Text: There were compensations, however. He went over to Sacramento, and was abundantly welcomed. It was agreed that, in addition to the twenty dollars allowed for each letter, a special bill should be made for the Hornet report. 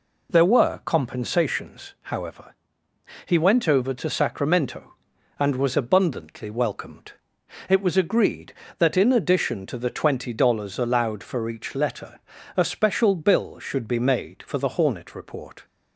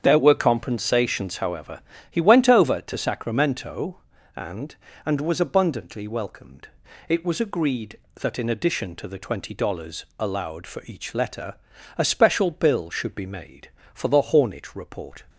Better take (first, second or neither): first